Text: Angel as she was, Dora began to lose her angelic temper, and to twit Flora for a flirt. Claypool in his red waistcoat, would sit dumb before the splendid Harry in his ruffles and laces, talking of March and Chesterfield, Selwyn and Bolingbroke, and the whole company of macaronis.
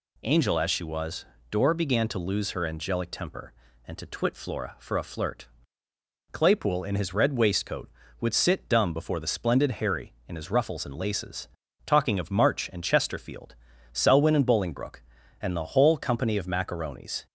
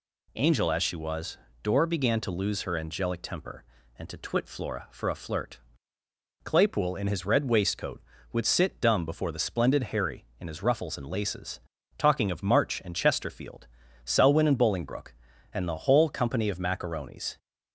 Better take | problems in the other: neither | none

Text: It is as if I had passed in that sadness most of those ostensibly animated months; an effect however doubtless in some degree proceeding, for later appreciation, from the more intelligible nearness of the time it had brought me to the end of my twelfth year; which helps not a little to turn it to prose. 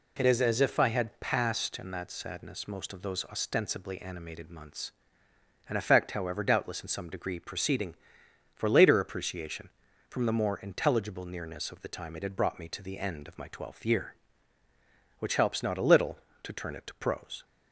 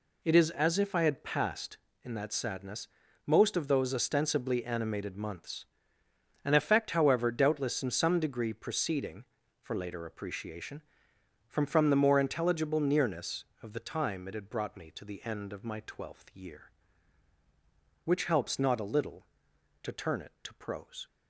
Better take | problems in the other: first | pauses between "sadness" and "most"; at 2.8 s; 0.38 s long // says "from" twice; at 11.6 s

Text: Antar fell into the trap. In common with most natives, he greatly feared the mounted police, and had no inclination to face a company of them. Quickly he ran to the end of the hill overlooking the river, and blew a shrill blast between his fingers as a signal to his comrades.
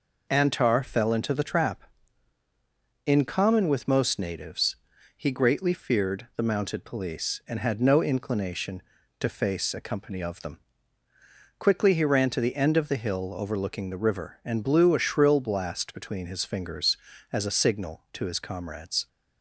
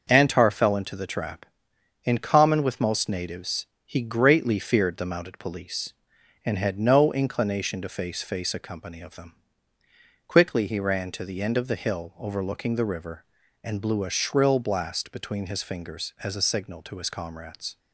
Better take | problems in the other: first | says "face" twice; at 8.2 s

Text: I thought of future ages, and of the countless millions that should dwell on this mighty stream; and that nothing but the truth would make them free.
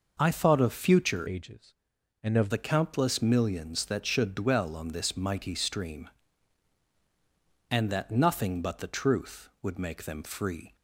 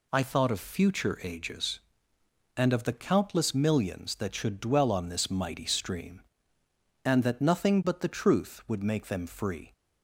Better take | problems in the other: second | changes voice from "ages" to "of"; from 1.2 to 2.4 s; 1.2 s long

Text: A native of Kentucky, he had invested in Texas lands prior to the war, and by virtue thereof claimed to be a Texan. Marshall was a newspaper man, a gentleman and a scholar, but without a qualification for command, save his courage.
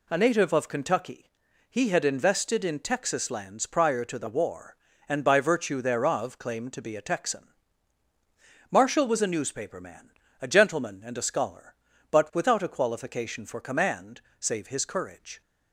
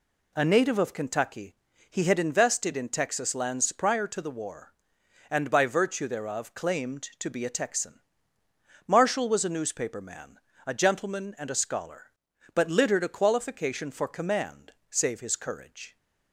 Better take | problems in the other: first | says "littered" for "without"; at 12.6 s

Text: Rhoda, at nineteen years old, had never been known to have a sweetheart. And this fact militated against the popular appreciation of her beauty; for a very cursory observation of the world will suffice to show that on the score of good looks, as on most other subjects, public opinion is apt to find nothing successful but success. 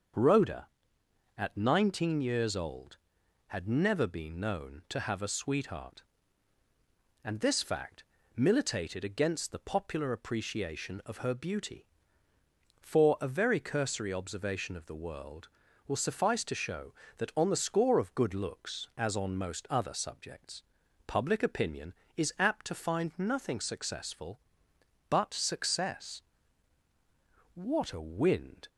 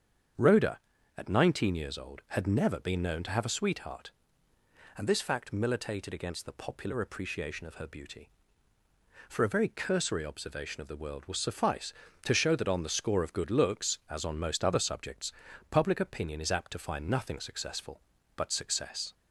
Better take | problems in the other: second | starts louder than the rest; until 1.8 s; 6.5 dB; strong in the second // pauses between "fact" and "militated"; slight; at 8.0 s; 0.32 s long // goes on to say "What a wind"; noticeable; from 27.5 s on; 1.1 s long

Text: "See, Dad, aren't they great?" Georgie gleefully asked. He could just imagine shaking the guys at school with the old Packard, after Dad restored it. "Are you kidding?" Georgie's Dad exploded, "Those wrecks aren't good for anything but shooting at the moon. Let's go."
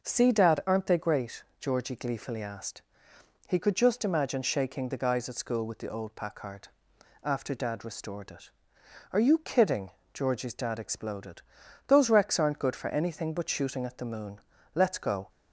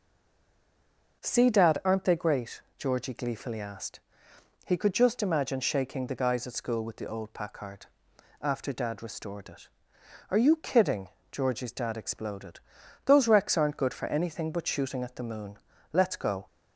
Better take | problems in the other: first | stays silent before the first word; noticeable; until 1.2 s; 1.2 s long

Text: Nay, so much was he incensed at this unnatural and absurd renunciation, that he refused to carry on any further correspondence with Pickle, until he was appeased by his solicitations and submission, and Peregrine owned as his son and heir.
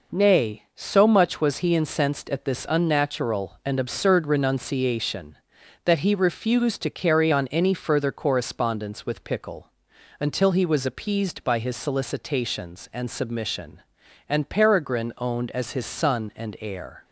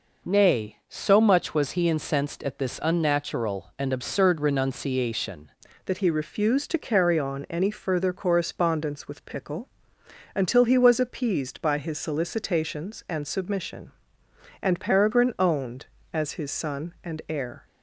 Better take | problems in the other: first | changes voice at "that"; from 5.8 s on; 11.8 s long

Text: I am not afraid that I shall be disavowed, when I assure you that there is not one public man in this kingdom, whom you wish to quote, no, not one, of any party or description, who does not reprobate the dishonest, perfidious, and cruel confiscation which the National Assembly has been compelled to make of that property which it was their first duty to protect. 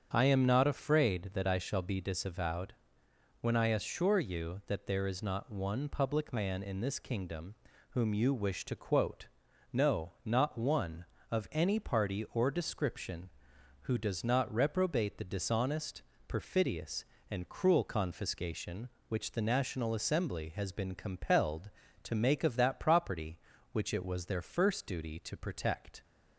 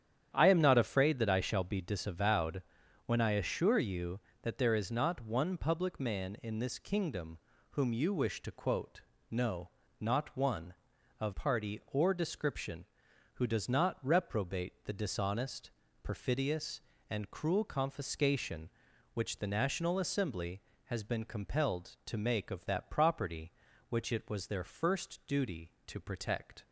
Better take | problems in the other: first | starts louder than the rest; strong; until 1.3 s; 9.5 dB; strong in the first // skips "any"; at 11.3 s

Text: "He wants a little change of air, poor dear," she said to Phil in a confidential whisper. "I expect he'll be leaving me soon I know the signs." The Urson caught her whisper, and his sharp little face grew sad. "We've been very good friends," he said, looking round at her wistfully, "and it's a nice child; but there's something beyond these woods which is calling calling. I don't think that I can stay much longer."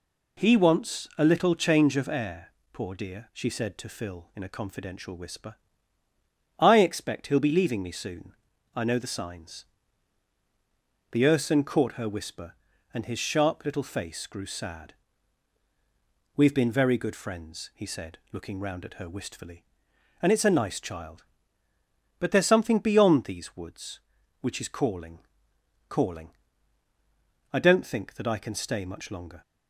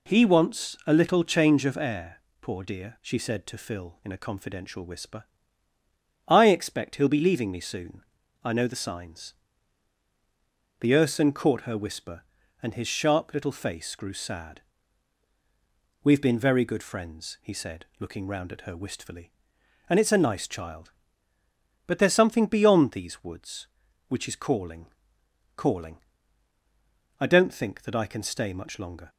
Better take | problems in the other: neither | pauses between "soon" and "I"; the same in both // pauses between "calling" and "calling"; noticeable; the same in both

